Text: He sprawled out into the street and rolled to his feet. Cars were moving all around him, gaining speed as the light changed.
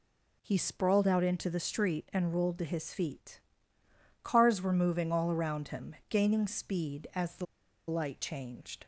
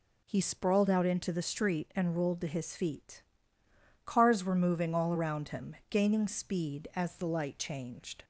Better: second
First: pauses between "the" and "light"; at 7.4 s; 0.44 s long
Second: none

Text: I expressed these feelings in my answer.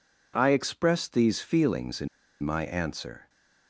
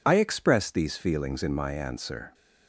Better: second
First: pauses between "in" and "my"; slight; at 2.0 s; 0.35 s long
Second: none

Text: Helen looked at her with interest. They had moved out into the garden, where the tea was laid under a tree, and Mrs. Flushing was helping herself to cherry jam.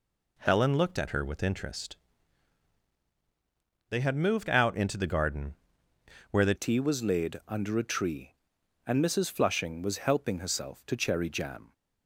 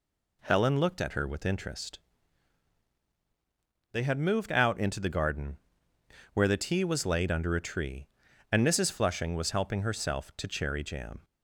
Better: second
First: changes voice at "tea"; from 6.5 s on; 5.2 s long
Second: none

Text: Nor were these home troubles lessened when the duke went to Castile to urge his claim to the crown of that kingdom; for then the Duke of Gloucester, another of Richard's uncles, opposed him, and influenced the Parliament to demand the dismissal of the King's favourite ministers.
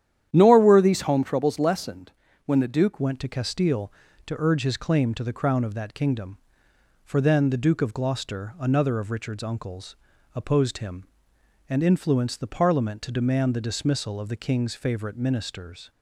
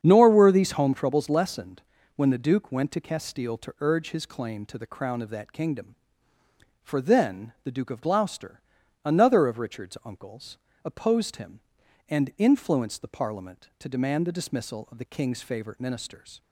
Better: second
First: starts louder than the rest; strong; until 1.3 s; 10.5 dB // pauses between "lessened" and "when"; slight; at 2.1 s; 0.34 s long // changes voice at "went"; from 3.0 s on; 12.9 s long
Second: starts louder than the rest; strong; until 1.0 s; 8 dB // pauses between "lessened" and "when"; slight; at 1.8 s; 0.34 s long

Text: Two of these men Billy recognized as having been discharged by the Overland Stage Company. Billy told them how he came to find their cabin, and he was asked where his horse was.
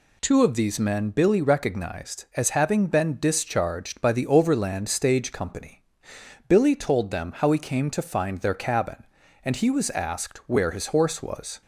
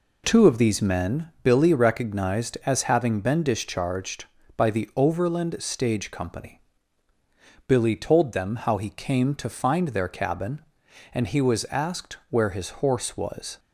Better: neither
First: none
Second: none

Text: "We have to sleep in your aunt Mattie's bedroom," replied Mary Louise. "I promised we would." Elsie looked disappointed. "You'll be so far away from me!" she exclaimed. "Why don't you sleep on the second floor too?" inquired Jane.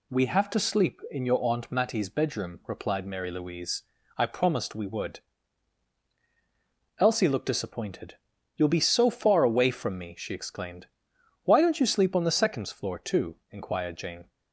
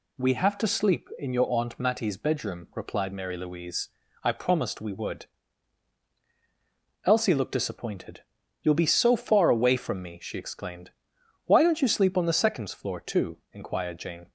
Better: neither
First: none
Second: none

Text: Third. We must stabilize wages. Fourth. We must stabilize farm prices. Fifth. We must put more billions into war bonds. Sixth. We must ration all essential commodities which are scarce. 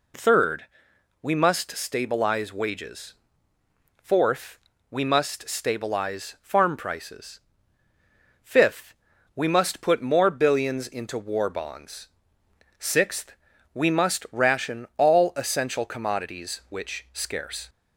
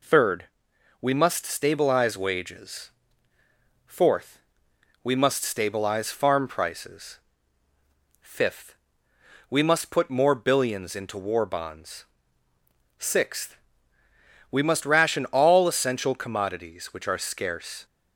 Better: second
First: skips "are"; at 17.0 s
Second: none

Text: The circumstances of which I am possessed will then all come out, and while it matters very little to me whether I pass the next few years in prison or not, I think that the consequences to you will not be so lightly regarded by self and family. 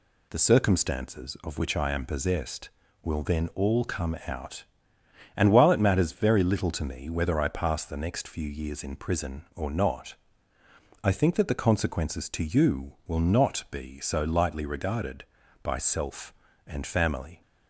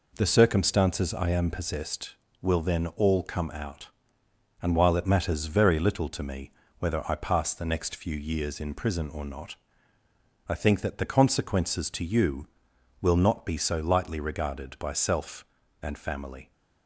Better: first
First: none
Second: skips "of which"; at 1.1 s // pauses between "me" and "whether"; slight; at 6.5 s; 0.26 s long

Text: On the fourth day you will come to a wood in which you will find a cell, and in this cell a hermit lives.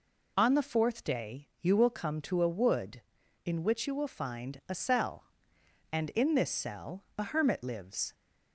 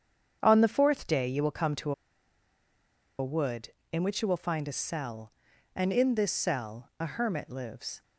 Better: first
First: none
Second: starts louder than the rest; strong; until 1.4 s; 7.5 dB // pauses between "to" and "a"; strong; at 1.9 s; 1.2 s long

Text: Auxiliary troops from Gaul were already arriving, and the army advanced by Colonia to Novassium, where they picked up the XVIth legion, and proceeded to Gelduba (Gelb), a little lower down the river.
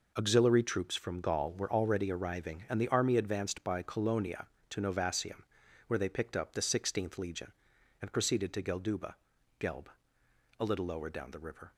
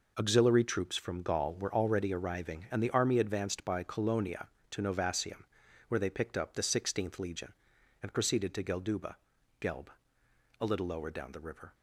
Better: neither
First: none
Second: none

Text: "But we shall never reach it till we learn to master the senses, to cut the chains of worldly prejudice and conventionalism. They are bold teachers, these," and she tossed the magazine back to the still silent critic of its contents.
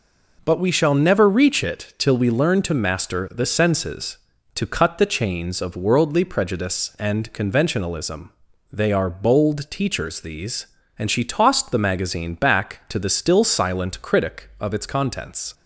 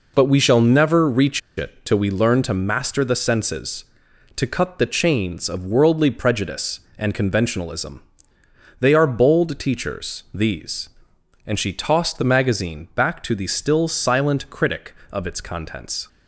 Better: first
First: none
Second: pauses between "reach" and "it"; slight; at 1.4 s; 0.17 s long

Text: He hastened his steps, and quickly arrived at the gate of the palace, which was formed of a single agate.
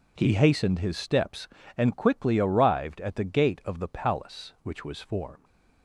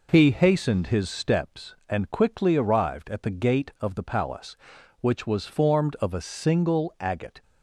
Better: second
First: stops before "of a single agate"; at 5.4 s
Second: none

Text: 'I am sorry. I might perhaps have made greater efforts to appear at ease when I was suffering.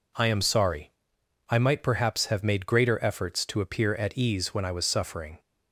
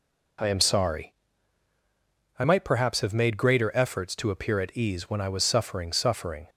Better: first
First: none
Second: says "suffering" twice; at 5.9 s

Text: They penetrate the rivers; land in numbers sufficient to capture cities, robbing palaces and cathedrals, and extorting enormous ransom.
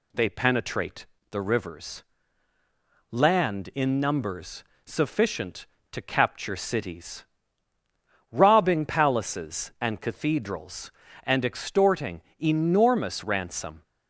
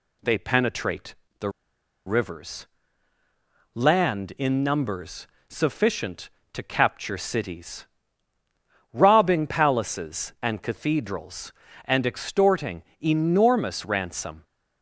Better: first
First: pauses between "penetrate" and "the"; slight; at 1.0 s; 0.24 s long // pauses between "numbers" and "sufficient"; slight; at 4.6 s; 0.20 s long // pauses between "extorting" and "enormous"; slight; at 12.2 s; 0.18 s long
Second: pauses between "penetrate" and "the"; slight; at 1.1 s; 0.24 s long // pauses between "the" and "rivers"; noticeable; at 1.4 s; 0.57 s long // pauses between "numbers" and "sufficient"; slight; at 5.2 s; 0.20 s long // pauses between "extorting" and "enormous"; slight; at 12.8 s; 0.18 s long

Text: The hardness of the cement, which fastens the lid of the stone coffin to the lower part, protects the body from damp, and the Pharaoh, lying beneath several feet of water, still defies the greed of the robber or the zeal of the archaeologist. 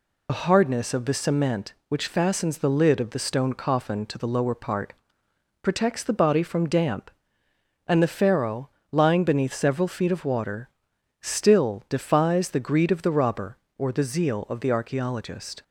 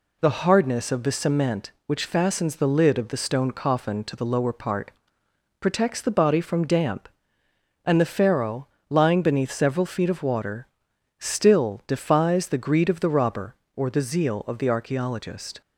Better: second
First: loses the start of "The"; at 0.2 s; 70 ms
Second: none

